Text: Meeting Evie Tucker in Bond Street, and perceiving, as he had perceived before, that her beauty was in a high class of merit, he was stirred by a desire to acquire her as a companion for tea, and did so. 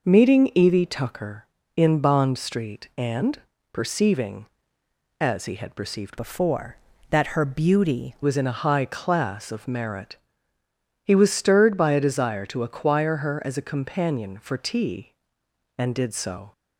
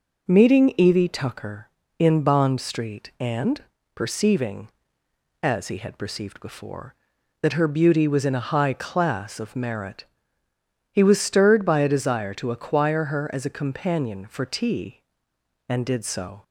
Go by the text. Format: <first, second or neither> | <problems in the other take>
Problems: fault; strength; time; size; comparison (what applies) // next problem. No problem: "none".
second | pauses between "and" and "perceiving"; slight; at 3.3 s; 0.34 s long; slight in the second // changes voice from "before" to "beauty"; from 6.1 to 8.1 s; 2.0 s long